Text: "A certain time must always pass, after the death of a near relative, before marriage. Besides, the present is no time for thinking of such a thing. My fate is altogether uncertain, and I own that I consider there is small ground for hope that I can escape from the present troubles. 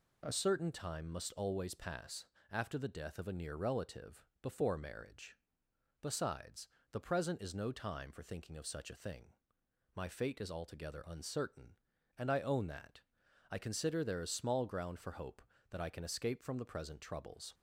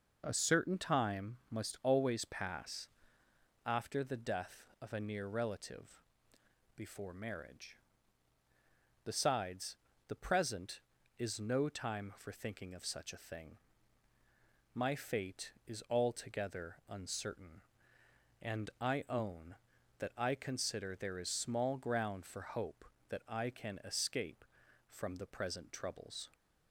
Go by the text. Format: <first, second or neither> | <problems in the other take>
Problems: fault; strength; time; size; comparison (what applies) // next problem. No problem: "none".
second | changes voice at "certain"; from 0.3 s on; 17.2 s long // pauses between "that" and "I"; noticeable; at 13.0 s; 0.48 s long